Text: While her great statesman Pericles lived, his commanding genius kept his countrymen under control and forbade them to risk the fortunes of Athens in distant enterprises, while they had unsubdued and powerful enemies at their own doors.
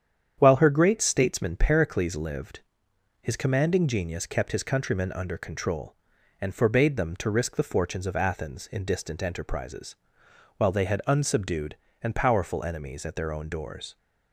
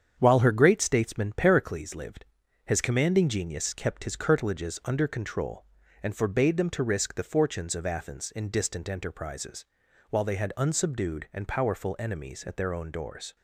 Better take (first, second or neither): first